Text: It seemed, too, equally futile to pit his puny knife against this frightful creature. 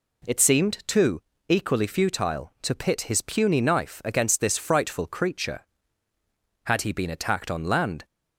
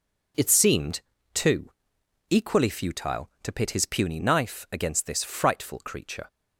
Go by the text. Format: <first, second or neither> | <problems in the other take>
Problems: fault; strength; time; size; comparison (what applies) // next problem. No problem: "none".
second | goes on to say "Had he been attacked on land"; from 6.6 s on; 1.4 s long